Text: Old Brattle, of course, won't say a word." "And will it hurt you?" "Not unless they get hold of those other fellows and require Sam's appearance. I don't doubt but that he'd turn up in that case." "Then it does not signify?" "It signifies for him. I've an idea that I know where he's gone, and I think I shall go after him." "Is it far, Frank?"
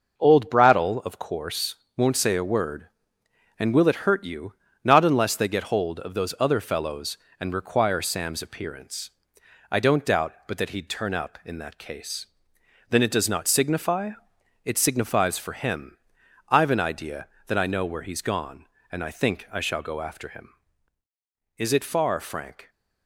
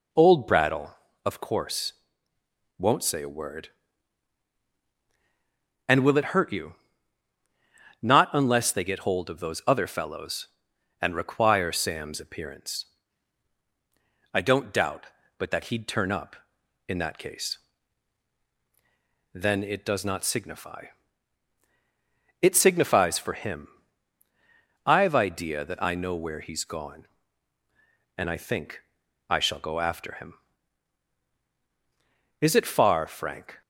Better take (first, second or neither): first